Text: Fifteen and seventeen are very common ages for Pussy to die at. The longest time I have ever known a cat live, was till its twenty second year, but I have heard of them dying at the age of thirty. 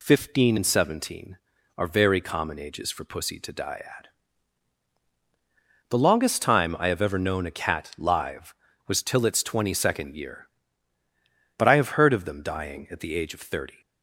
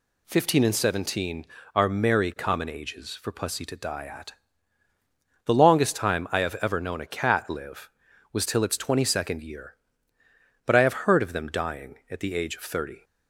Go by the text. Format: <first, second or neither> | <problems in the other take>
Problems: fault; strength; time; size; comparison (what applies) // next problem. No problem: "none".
first | says "merry" for "very"; at 1.8 s